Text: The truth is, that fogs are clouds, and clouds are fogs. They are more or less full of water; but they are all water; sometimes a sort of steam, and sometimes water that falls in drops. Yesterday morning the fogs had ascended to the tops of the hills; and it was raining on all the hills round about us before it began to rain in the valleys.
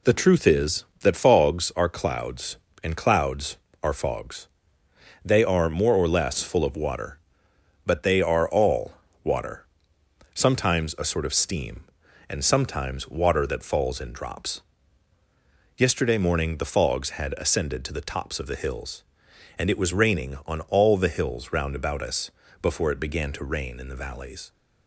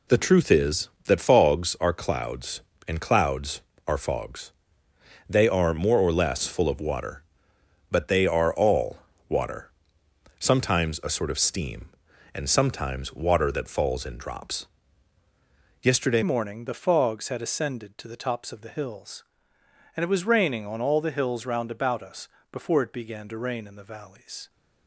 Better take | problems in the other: first | pauses between "all" and "water"; slight; at 8.9 s; 0.32 s long; slight in the first // changes voice at "morning"; from 16.2 s on; 8.2 s long // pauses between "us" and "before"; slight; at 22.2 s; 0.24 s long; slight in the first

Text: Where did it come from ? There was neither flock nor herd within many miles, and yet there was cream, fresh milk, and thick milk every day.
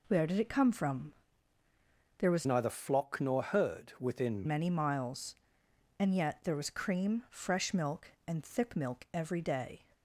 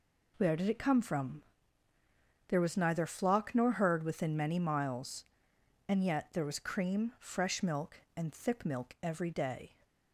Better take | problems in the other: second | changes voice from "neither" to "within"; from 2.4 to 4.4 s; 2.0 s long

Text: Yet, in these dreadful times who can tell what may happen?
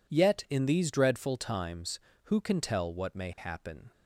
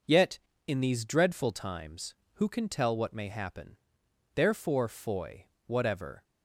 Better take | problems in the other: first | goes on to say "Therefore Foy whatever"; strong; from 4.3 s on; 1.9 s long

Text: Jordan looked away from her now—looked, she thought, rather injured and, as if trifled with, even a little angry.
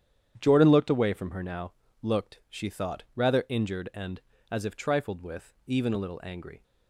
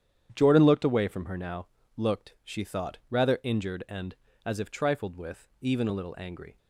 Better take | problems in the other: neither | starts louder than the rest; strong; the same in both

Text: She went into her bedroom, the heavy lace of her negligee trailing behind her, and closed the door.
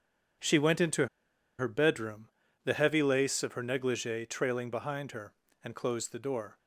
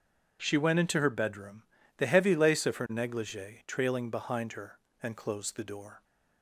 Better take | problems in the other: second | starts louder than the rest; strong; until 1.9 s; 8 dB // pauses between "into" and "her"; noticeable; at 1.0 s; 0.52 s long

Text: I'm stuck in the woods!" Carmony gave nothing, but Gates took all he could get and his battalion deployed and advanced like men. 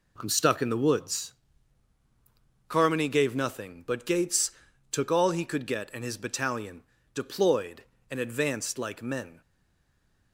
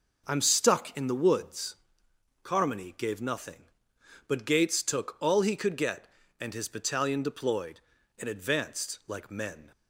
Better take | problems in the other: second | pauses between "Gates" and "took"; at 4.5 s; 0.40 s long // pauses between "battalion" and "deployed"; slight; at 6.8 s; 0.30 s long // stays silent after the last word; slight; from 9.4 s on; 0.9 s long

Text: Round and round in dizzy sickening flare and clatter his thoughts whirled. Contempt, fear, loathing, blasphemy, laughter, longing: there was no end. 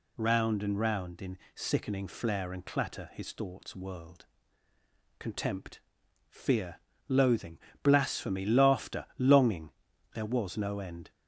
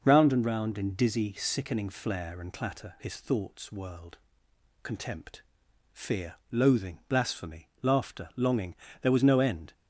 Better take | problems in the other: second | skips "dizzy"; at 1.4 s

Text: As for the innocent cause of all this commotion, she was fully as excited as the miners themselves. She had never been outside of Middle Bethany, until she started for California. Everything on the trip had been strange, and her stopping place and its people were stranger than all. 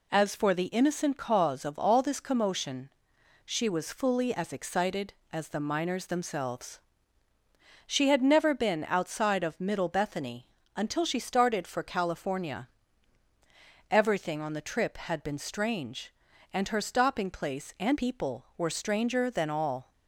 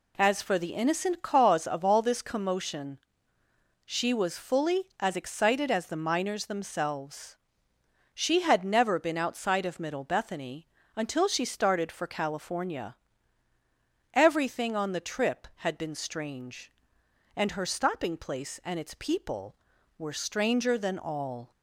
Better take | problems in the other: second | skips "its"; at 17.9 s

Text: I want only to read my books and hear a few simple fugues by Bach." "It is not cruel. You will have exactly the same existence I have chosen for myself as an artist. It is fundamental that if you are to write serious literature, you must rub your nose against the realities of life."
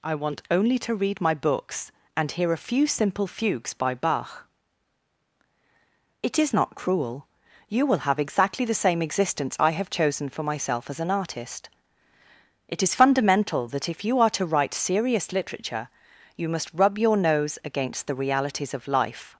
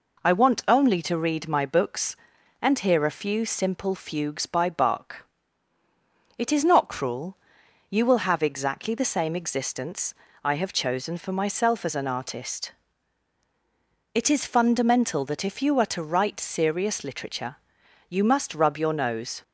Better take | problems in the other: first | pauses between "existence" and "I"; slight; at 10.1 s; 0.28 s long // stops before "against the realities of life"; at 19.4 s

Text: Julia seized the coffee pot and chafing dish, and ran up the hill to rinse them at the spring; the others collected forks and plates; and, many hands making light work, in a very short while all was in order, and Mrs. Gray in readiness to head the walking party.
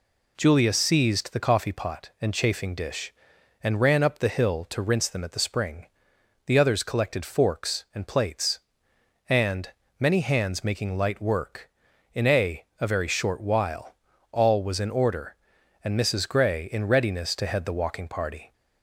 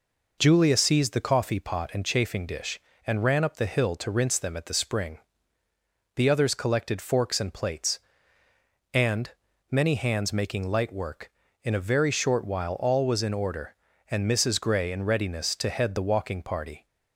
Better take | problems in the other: second | says "a" twice; at 12.7 s // pauses between "while" and "all"; slight; at 13.9 s; 0.36 s long

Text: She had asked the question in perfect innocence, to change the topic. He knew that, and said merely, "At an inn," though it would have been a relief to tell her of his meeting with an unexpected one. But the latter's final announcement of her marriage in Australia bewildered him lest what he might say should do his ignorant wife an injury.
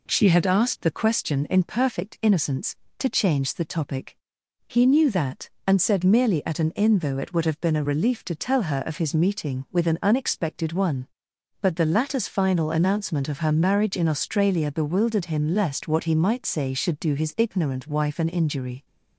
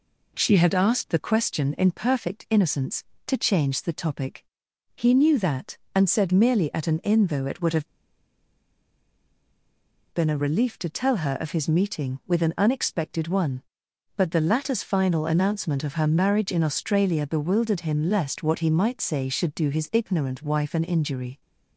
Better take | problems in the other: first | pauses between "have" and "been"; strong; at 7.8 s; 2.2 s long

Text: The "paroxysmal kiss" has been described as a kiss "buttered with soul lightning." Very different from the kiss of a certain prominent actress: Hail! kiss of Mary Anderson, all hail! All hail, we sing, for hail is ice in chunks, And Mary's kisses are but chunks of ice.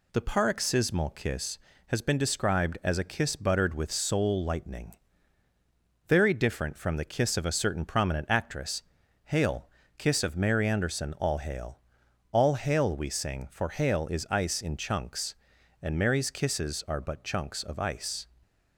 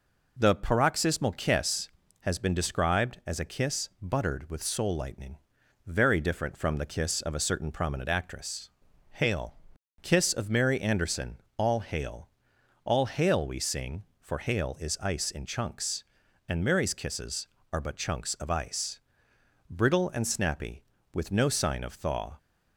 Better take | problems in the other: first | goes on to say "Brittle and snappy with no sign of thaw"; strong; from 19.7 s on; 2.6 s long

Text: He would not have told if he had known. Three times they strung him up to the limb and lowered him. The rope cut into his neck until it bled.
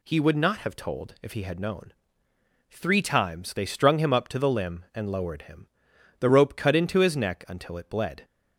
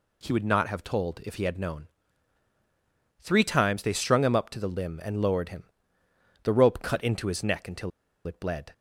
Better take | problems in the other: first | pauses between "until" and "it"; at 7.9 s; 0.36 s long

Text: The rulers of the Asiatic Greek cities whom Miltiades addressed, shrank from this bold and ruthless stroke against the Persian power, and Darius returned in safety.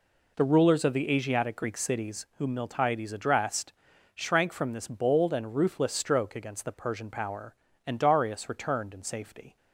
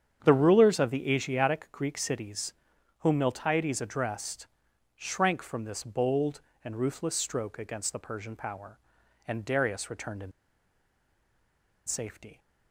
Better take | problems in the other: first | starts louder than the rest; strong; until 1.2 s; 8.5 dB // pauses between "cities" and "whom"; noticeable; at 2.5 s; 0.46 s long // pauses between "in" and "safety"; strong; at 10.3 s; 1.5 s long

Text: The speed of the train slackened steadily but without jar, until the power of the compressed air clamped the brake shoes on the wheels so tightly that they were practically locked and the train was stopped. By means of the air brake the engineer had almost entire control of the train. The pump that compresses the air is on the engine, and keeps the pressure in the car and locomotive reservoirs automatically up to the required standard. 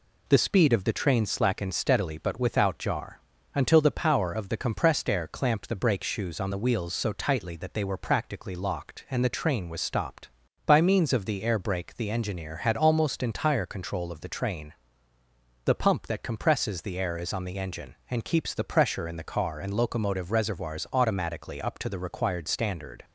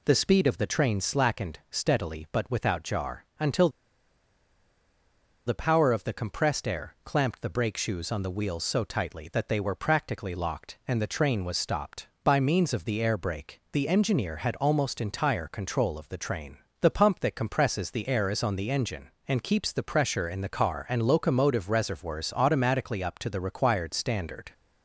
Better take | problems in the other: first | pauses between "until" and "the"; strong; at 3.6 s; 1.7 s long

